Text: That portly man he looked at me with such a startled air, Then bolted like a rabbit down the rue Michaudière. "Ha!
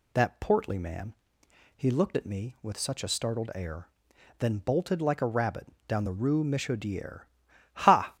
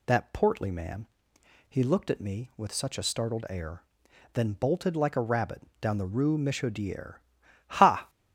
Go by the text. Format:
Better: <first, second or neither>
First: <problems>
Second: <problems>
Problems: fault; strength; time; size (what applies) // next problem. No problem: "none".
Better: neither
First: pauses between "man" and "he"; noticeable; at 1.1 s; 0.60 s long // pauses between "rabbit" and "down"; slight; at 5.6 s; 0.20 s long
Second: pauses between "man" and "he"; noticeable; at 1.0 s; 0.60 s long // pauses between "rabbit" and "down"; slight; at 5.6 s; 0.18 s long